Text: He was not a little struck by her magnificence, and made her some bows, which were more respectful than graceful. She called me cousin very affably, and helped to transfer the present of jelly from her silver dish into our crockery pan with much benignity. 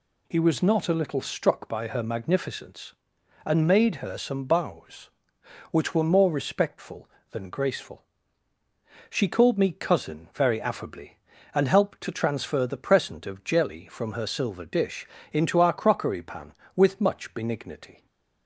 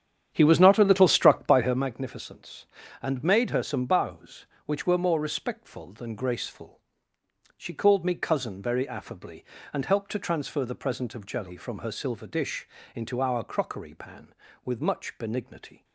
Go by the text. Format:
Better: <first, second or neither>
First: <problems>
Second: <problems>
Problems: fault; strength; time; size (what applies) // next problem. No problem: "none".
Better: first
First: pauses between "dish" and "into"; slight; at 15.0 s; 0.24 s long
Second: starts louder than the rest; strong; until 1.8 s; 9 dB // pauses between "dish" and "into"; slight; at 12.6 s; 0.30 s long